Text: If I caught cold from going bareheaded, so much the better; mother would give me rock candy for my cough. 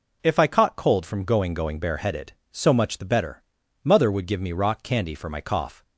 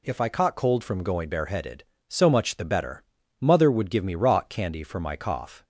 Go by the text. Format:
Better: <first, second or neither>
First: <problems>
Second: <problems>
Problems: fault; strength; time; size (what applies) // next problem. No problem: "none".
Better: second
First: says "going" twice; at 1.5 s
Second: none